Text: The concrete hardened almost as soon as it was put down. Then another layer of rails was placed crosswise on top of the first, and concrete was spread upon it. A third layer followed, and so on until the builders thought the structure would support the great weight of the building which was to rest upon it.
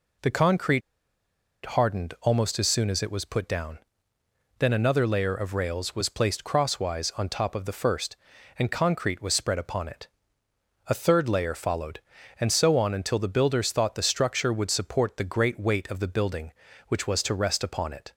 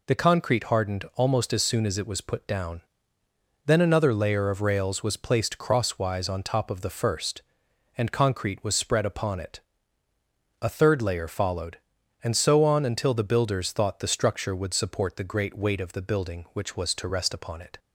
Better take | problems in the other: second | pauses between "concrete" and "hardened"; noticeable; at 0.8 s; 0.83 s long

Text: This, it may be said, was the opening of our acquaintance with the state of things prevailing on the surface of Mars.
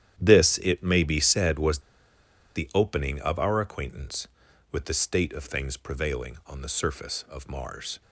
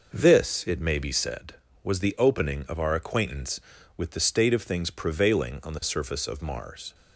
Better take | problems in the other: second | starts louder than the rest; strong; until 1.2 s; 10.5 dB // pauses between "was" and "the"; noticeable; at 1.7 s; 0.76 s long

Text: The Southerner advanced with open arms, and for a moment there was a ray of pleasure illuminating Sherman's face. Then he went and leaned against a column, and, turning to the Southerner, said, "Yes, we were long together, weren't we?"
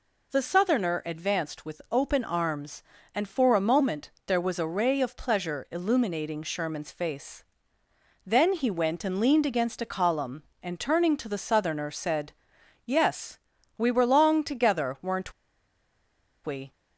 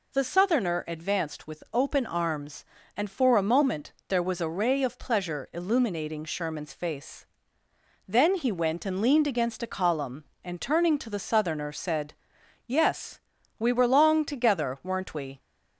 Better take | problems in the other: second | pauses between "moment" and "there"; slight; at 4.0 s; 0.16 s long; slight in the second // pauses between "weren't" and "we"; at 15.3 s; 1.1 s long

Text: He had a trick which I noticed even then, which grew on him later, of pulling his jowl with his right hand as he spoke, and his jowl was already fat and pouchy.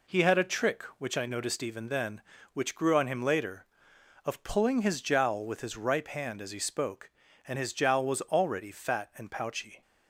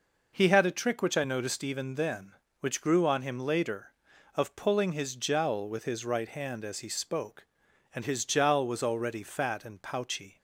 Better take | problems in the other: second | says "ripe" for "right"; at 5.7 s

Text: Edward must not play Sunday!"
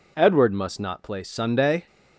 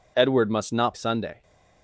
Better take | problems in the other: first | skips "play"; at 0.9 s

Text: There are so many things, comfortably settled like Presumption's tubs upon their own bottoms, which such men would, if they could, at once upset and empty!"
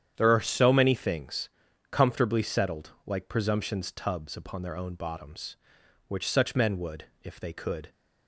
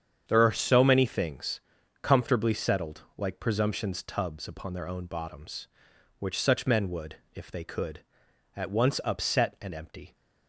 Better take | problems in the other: second | starts louder than the rest; strong; until 1.1 s; 9 dB; strong in the second // pauses between "settled" and "like"; slight; at 2.9 s; 0.16 s long; slight in the second // stops before "at once upset and empty"; at 7.9 s

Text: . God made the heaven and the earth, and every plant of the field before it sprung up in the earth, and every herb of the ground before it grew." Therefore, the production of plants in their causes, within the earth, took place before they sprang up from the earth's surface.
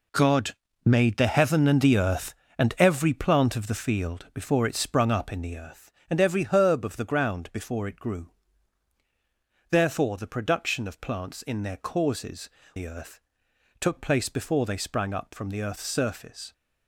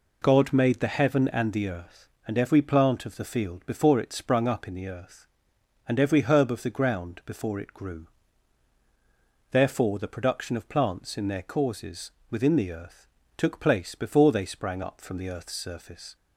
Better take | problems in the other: second | pauses between "God" and "made"; slight; at 0.5 s; 0.28 s long // skips "within"; at 12.6 s

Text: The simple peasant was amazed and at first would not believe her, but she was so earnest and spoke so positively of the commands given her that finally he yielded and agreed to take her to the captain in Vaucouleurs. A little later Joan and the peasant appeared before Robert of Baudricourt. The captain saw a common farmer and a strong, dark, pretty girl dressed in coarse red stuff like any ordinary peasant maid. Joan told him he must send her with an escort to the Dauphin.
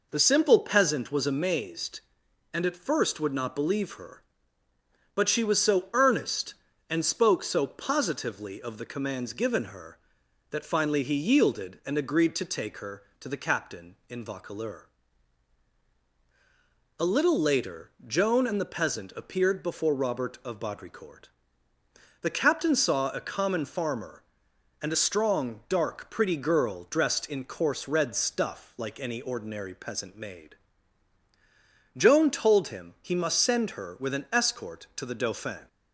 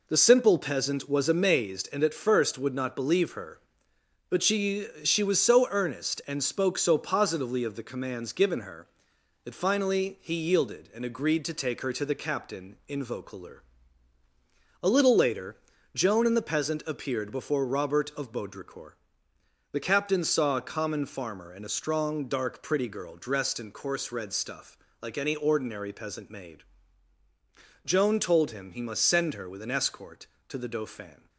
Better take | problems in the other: first | says "she" twice; at 5.0 s // pauses between "later" and "Joan"; at 15.5 s; 0.40 s long; slight in the first // pauses between "stuff" and "like"; slight; at 24.7 s; 0.24 s long

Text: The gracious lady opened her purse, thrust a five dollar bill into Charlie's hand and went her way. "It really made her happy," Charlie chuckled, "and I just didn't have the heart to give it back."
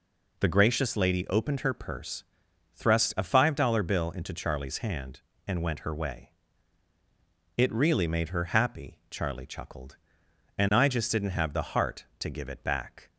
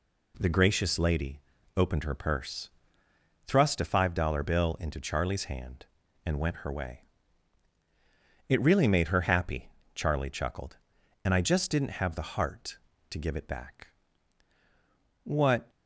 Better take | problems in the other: first | pauses between "lady" and "opened"; at 1.3 s; 0.38 s long // goes on to say "What"; slight; from 15.2 s on; 0.48 s long

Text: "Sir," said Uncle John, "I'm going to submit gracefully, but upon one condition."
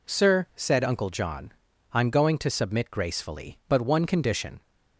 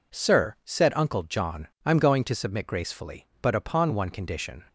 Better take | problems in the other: second | skips "upon"; at 3.8 s

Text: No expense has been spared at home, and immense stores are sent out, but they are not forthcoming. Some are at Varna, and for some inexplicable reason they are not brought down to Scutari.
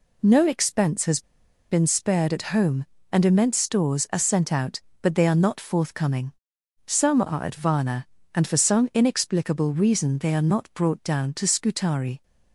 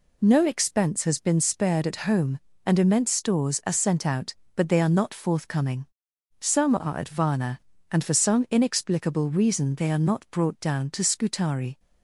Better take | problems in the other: second | pauses between "has" and "been"; noticeable; at 1.2 s; 0.47 s long

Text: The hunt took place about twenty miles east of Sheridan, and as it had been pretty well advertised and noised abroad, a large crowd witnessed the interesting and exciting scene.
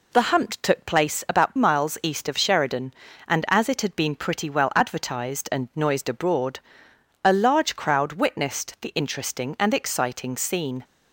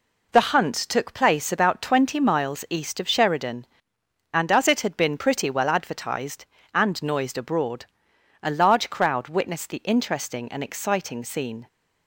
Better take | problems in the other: second | skips "twenty"; at 1.5 s

